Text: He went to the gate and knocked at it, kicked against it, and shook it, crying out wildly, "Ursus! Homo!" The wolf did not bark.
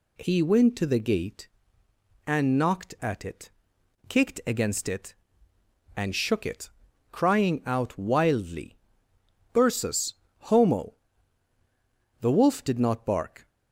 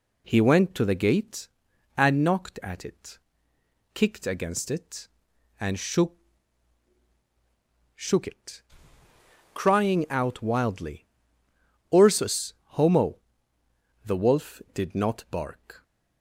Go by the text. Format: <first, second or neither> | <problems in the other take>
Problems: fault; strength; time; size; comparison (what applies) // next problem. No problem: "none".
first | says "shook" twice; at 7.9 s